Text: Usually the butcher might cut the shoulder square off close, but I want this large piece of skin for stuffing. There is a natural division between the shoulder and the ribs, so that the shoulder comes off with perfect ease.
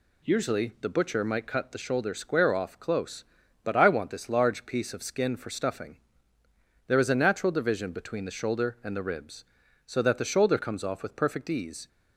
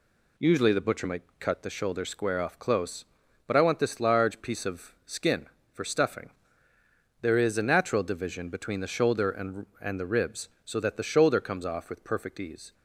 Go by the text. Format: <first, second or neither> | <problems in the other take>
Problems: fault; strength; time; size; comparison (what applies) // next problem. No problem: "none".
first | pauses between "might" and "cut"; slight; at 1.2 s; 0.16 s long // says "and" twice; at 9.8 s